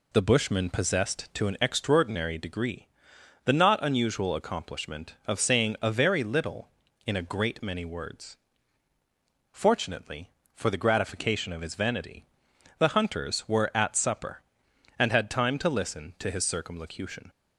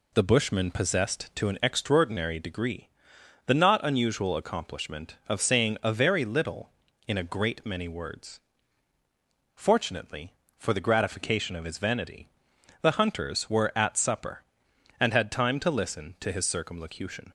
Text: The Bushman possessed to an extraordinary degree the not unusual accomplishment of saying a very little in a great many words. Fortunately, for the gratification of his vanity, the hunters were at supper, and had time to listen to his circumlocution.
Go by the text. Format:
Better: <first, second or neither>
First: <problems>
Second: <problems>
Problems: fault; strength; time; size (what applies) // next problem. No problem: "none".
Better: neither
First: pauses between "degree" and "the"; noticeable; at 2.8 s; 0.58 s long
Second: pauses between "degree" and "the"; noticeable; at 2.8 s; 0.58 s long